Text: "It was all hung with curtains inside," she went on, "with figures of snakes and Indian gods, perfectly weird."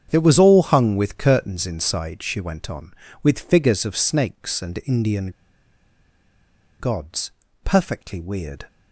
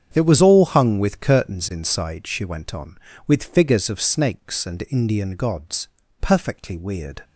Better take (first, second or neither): second